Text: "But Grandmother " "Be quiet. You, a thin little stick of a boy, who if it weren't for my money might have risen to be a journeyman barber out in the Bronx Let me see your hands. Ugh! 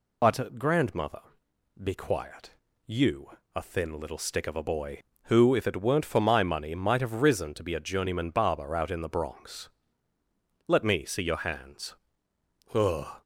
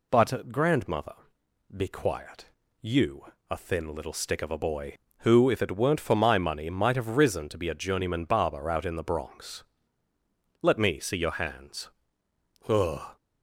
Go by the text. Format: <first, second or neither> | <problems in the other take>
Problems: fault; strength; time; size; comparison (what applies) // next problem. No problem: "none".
second | loses the start of "But"; at 0.2 s; 50 ms // pauses between "Bronx" and "Let"; noticeable; at 9.6 s; 0.98 s long; noticeable in the second